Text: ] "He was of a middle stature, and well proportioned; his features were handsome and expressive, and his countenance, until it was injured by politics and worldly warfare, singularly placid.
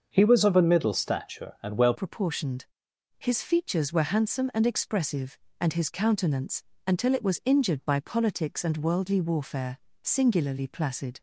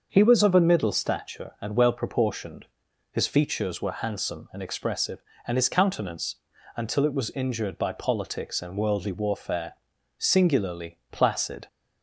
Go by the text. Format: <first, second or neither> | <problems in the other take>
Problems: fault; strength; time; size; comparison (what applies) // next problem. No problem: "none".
second | starts louder than the rest; until 1.1 s; 6.5 dB; also in the second // changes voice at "proportioned"; from 1.9 s on; 9.2 s long